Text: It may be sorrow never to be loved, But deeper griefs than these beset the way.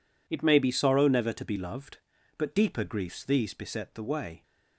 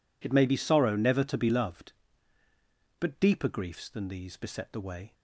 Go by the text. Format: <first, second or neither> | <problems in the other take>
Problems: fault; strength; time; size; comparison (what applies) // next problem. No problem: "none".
second | skips "than"; at 3.2 s